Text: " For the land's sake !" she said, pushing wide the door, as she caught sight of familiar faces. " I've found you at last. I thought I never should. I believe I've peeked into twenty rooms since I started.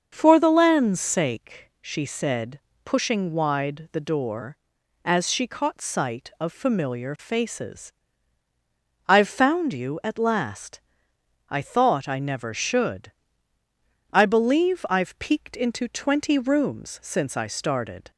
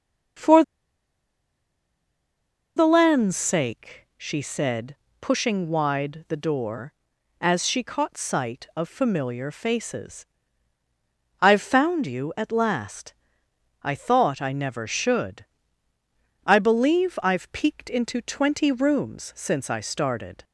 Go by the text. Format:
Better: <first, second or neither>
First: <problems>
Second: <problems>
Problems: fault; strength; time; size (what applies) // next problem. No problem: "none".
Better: first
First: starts louder than the rest; until 1.1 s; 6.5 dB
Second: starts louder than the rest; until 3.5 s; 6.5 dB // pauses between "For" and "the"; strong; at 0.6 s; 2.1 s long